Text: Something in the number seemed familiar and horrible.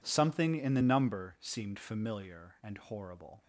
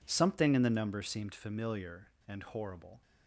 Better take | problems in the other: neither | none

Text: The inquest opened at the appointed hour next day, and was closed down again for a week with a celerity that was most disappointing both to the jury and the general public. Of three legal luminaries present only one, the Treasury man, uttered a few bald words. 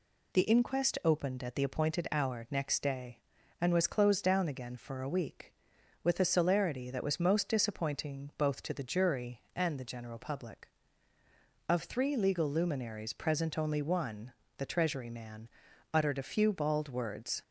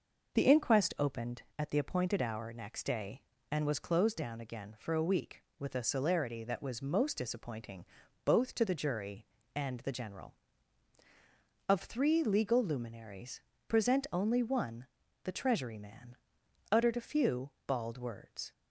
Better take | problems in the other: first | pauses between "disappointing" and "both"; at 7.8 s; 0.40 s long // skips "public"; at 11.0 s // pauses between "luminaries" and "present"; slight; at 13.4 s; 0.26 s long // pauses between "few" and "bald"; slight; at 17.4 s; 0.18 s long

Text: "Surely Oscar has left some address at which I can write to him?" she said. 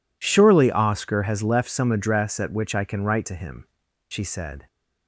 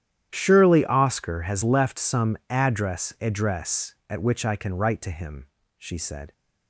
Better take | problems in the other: first | starts louder than the rest; strong; until 1.3 s; 11 dB // says "address" twice; at 3.1 s

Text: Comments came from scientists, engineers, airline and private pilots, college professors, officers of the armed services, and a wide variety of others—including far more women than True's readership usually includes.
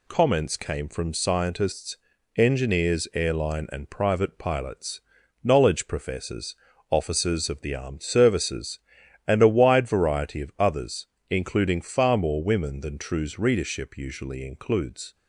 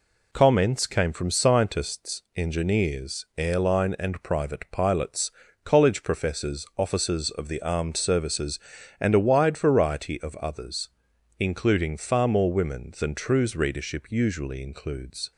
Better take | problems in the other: second | says "knowledge" for "college"; at 5.4 s

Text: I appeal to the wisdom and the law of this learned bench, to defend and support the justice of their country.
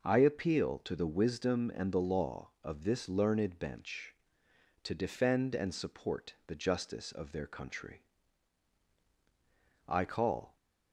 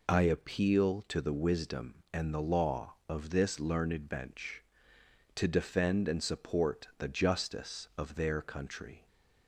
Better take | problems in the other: second | goes on to say "I call"; noticeable; from 9.8 s on; 0.70 s long

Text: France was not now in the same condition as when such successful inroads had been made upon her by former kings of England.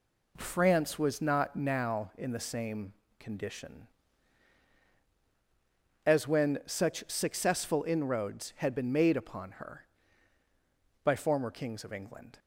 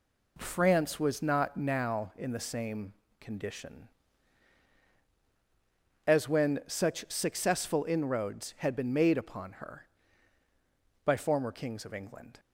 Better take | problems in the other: neither | pauses between "same" and "condition"; slight; the same in both

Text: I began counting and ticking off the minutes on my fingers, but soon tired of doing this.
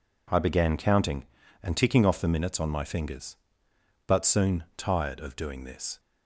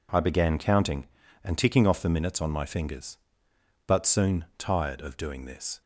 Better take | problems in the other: neither | none

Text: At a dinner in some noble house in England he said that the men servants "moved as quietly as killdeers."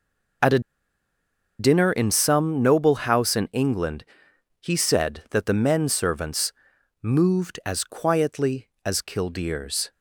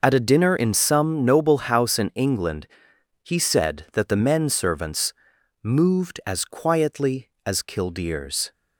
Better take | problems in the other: second | pauses between "a" and "dinner"; at 0.5 s; 0.99 s long // pauses between "England" and "he"; noticeable; at 4.0 s; 0.56 s long; noticeable in the second // pauses between "servants" and "moved"; noticeable; at 6.5 s; 0.48 s long; noticeable in the second

